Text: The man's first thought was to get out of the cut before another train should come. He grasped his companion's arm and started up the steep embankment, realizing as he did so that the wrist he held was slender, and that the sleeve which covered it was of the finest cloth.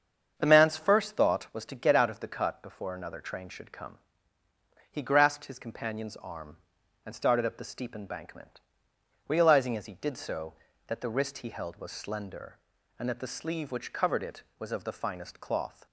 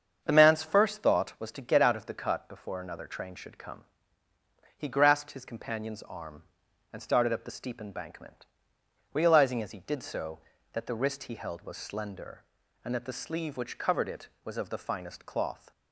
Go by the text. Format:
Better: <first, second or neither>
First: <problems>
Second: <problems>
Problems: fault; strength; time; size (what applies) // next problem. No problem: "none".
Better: neither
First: starts louder than the rest; until 1.3 s; 7 dB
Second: starts louder than the rest; until 1.2 s; 7 dB